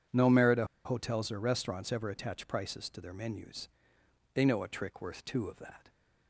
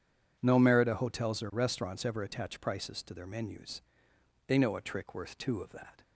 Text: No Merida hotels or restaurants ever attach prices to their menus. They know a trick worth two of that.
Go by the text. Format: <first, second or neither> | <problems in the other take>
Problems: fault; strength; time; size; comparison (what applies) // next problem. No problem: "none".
second | pauses between "Merida" and "hotels"; slight; at 0.6 s; 0.20 s long